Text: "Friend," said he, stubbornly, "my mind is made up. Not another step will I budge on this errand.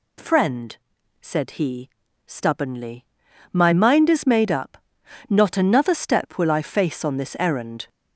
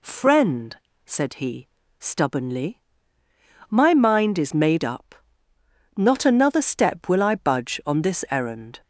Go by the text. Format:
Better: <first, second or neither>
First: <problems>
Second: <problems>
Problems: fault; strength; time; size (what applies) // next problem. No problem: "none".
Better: second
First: says "face" for "budge"; at 6.6 s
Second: none